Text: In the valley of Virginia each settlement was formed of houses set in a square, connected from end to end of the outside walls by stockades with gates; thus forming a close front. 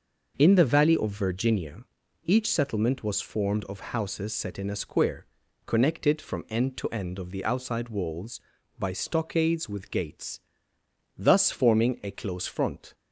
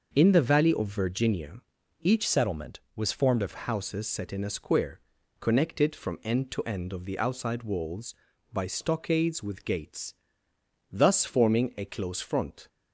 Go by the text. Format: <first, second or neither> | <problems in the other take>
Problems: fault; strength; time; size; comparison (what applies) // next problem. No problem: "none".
first | starts louder than the rest; noticeable; until 1.1 s; 6 dB // pauses between "Virginia" and "each"; at 1.6 s; 0.42 s long; also in the first // changes voice from "settlement" to "of"; from 2.2 to 3.5 s; 1.3 s long